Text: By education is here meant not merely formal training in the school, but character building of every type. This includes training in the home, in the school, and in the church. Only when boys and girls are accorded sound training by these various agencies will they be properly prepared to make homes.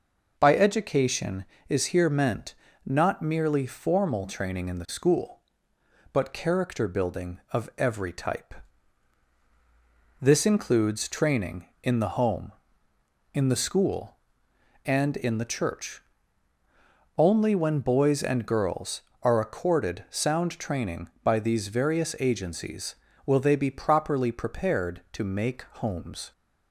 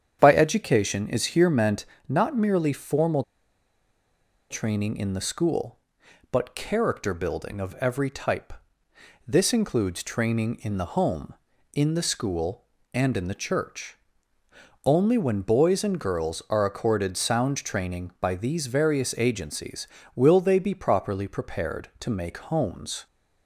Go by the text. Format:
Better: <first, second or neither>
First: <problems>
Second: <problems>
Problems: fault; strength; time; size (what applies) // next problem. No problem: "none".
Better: first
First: pauses between "meant" and "not"; slight; at 2.5 s; 0.30 s long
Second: starts louder than the rest; strong; until 1.2 s; 8.5 dB // pauses between "meant" and "not"; slight; at 1.8 s; 0.20 s long // pauses between "formal" and "training"; strong; at 3.2 s; 1.2 s long